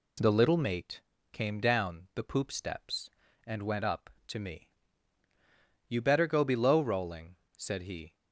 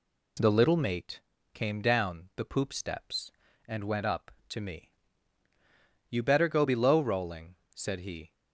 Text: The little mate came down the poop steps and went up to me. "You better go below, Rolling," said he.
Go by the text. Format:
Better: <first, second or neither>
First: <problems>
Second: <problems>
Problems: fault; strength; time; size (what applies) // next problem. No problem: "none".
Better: neither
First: pauses between "mate" and "came"; slight; at 1.0 s; 0.30 s long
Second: pauses between "mate" and "came"; slight; at 1.1 s; 0.32 s long